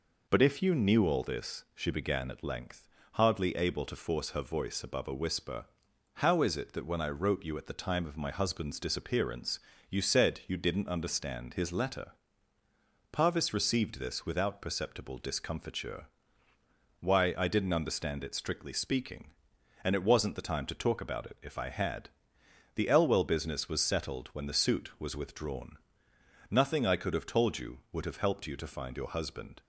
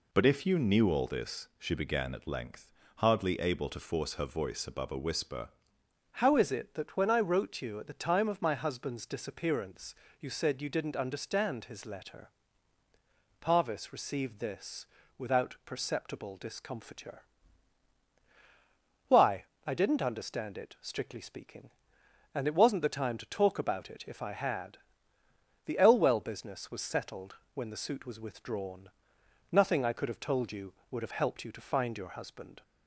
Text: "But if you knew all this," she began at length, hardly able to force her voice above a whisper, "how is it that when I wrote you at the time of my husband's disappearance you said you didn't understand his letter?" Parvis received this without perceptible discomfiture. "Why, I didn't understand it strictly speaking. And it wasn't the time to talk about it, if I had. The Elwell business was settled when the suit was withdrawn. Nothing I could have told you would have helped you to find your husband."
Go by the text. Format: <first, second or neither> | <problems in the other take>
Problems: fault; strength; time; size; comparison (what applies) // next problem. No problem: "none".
first | changes voice at "how"; from 6.1 s on; 26.5 s long // pauses between "disappearance" and "you"; slight; at 9.9 s; 0.26 s long; slight in the first // pauses between "this" and "without"; slight; at 14.8 s; 0.32 s long // pauses between "settled" and "when"; slight; at 27.3 s; 0.18 s long